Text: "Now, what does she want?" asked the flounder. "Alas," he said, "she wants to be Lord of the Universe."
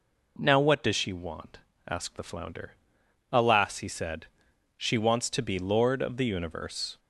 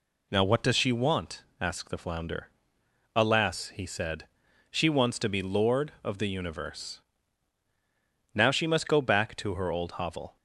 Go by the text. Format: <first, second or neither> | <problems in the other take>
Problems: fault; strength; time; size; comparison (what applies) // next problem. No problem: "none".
first | goes on to say "Now she must go back to her old hovel"; strong; from 8.3 s on; 2.0 s long